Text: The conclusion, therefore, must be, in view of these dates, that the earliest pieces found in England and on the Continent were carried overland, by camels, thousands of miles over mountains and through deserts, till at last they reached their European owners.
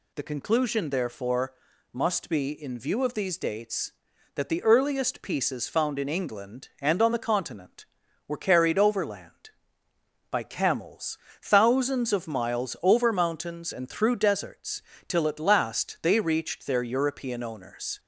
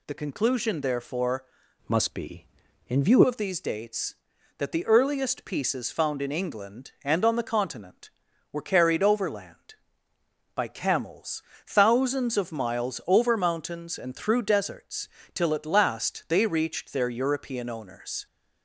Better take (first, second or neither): first